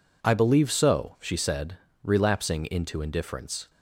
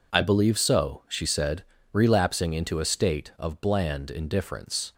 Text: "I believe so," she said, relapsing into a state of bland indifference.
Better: second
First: skips "a state of bland"; at 2.9 s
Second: none

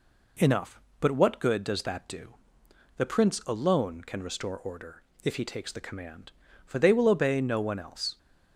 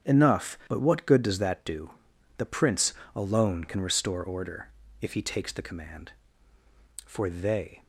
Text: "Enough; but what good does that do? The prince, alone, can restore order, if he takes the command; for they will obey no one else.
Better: first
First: none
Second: starts louder than the rest; strong; until 1.1 s; 8 dB // stops before "will obey no one else"; at 7.8 s

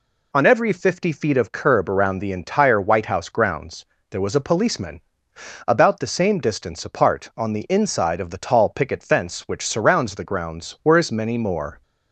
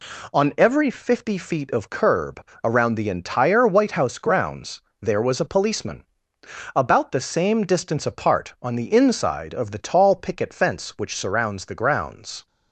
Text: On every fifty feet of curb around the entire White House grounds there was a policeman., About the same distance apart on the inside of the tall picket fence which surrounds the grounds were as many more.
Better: first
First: pauses between "grounds" and "there"; slight; at 3.8 s; 0.28 s long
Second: pauses between "curb" and "around"; slight; at 2.4 s; 0.20 s long // pauses between "grounds" and "there"; slight; at 4.8 s; 0.20 s long // stops before "were as many more"; at 12.4 s

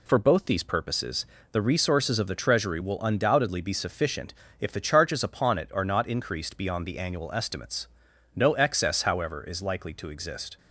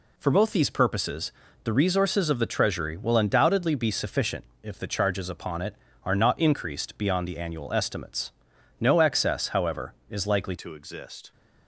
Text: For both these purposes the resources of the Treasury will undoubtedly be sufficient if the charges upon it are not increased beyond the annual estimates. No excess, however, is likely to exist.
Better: first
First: pauses between "purposes" and "the"; slight; at 1.2 s; 0.26 s long // pauses between "sufficient" and "if"; slight; at 4.3 s; 0.26 s long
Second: pauses between "purposes" and "the"; slight; at 1.3 s; 0.32 s long // pauses between "sufficient" and "if"; slight; at 4.4 s; 0.18 s long // changes voice at "to"; from 10.5 s on; 0.8 s long

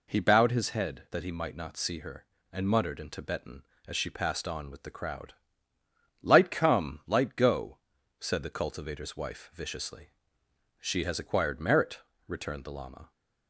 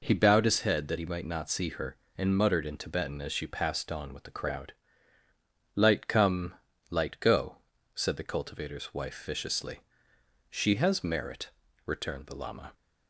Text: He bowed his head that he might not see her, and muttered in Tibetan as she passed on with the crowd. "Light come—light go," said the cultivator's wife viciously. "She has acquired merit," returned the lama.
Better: first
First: none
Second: skips "acquired"; at 11.0 s

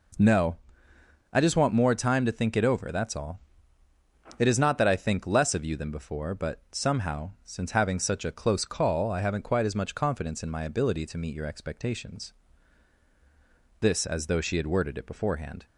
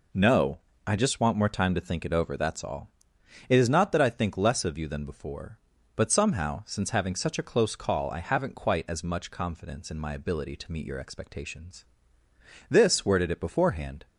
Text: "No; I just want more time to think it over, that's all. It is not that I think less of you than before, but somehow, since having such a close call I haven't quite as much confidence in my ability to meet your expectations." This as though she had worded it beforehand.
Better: first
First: none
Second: skips "as though she had"; at 13.0 s

